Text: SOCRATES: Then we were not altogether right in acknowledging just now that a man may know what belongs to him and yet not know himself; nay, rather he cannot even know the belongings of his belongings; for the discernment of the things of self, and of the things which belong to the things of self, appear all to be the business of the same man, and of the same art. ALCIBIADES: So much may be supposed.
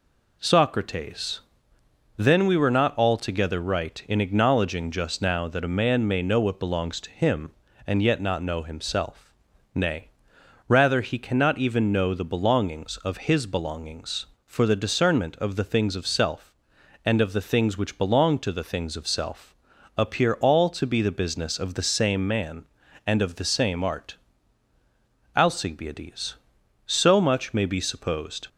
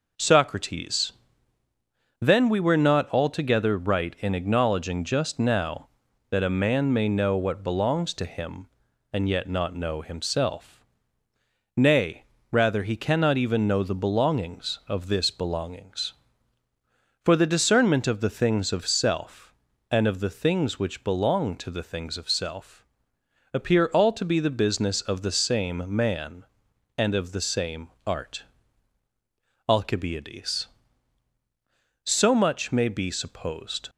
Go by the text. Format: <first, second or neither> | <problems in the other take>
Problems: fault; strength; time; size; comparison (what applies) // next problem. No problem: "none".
first | says "this" for "his"; at 15.0 s // pauses between "same" and "art"; slight; at 27.8 s; 0.18 s long